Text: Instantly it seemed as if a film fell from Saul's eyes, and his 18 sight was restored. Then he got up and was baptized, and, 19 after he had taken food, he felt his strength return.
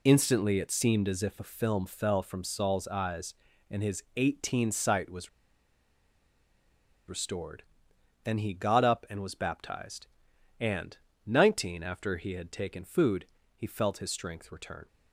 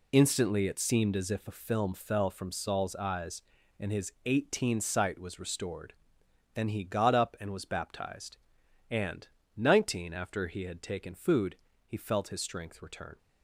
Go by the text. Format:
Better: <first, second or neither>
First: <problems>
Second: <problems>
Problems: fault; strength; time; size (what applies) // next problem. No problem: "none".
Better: second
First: pauses between "was" and "restored"; strong; at 5.2 s; 1.7 s long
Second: none